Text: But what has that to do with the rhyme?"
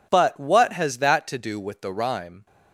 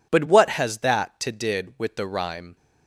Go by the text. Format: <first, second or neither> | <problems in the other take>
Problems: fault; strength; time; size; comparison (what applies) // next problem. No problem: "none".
first | says "did" for "do"; at 1.3 s